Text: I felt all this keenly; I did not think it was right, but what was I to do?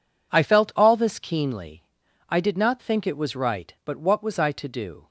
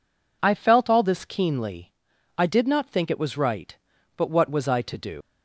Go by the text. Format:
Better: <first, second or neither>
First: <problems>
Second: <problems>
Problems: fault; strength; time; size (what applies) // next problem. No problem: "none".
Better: first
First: none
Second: leaves "do" unfinished; at 5.2 s; 120 ms